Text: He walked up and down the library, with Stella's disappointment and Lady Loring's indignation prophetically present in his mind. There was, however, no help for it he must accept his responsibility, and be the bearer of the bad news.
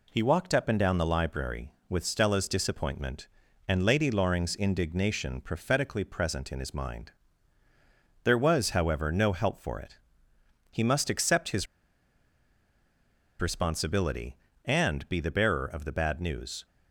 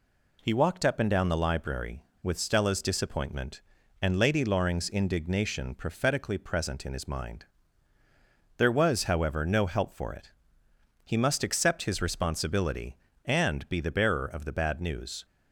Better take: second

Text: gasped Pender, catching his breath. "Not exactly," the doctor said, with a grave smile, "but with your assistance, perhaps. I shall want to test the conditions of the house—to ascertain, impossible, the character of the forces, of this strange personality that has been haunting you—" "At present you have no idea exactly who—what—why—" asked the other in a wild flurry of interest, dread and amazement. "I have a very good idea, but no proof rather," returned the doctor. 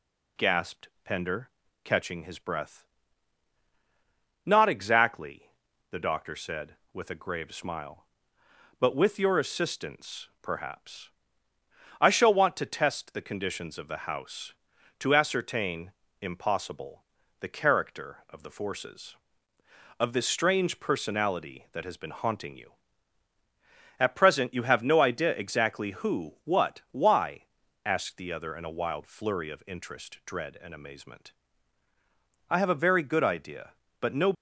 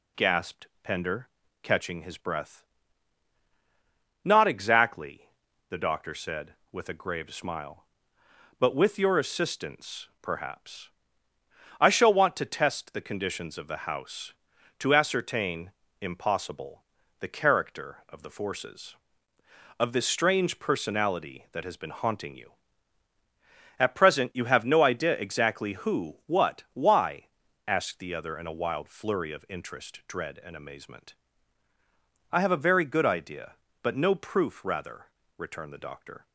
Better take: second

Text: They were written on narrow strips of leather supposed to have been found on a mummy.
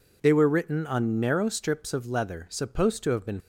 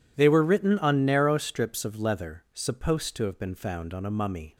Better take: second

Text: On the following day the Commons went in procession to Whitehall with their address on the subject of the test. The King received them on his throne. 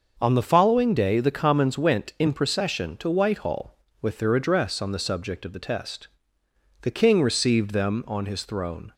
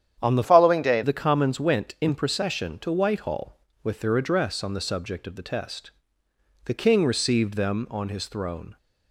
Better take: first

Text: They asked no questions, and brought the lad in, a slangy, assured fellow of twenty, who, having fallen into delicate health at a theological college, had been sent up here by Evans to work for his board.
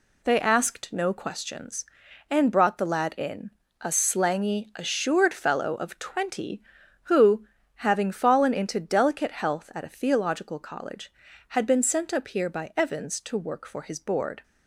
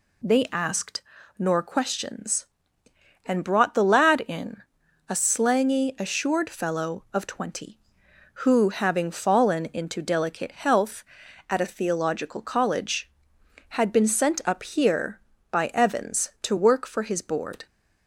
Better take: first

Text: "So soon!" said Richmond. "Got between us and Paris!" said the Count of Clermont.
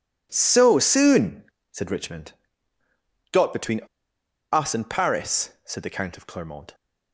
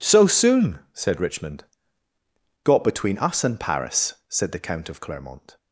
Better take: second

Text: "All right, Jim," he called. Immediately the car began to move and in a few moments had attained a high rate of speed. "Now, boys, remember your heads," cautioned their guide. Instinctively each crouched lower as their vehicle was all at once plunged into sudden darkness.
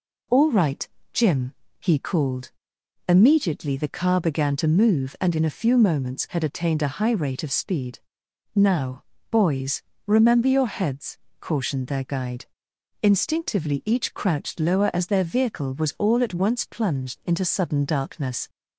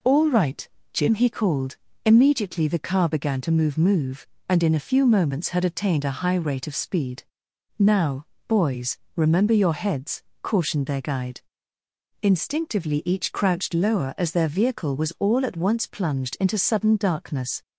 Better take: first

